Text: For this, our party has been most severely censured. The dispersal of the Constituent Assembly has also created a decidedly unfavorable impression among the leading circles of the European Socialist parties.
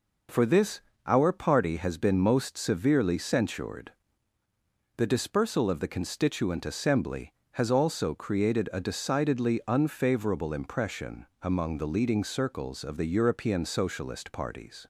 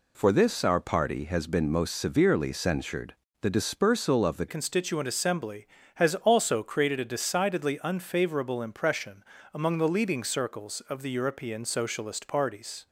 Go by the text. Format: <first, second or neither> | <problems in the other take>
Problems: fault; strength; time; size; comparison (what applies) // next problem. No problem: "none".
first | changes voice at "Constituent"; from 4.4 s on; 8.4 s long // pauses between "impression" and "among"; slight; at 9.2 s; 0.28 s long; slight in the first